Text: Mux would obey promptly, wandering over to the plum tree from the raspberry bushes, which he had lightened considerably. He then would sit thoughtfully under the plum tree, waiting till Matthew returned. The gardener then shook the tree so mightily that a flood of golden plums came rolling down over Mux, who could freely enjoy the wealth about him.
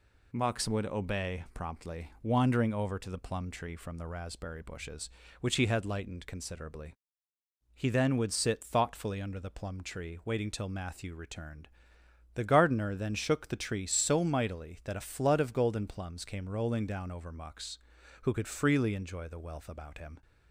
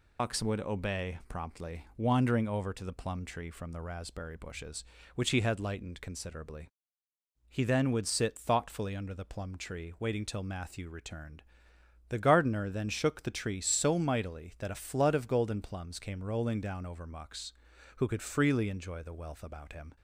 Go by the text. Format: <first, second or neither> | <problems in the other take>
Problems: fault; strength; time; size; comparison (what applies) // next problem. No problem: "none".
first | loses the start of "Mux"; at 0.1 s; 120 ms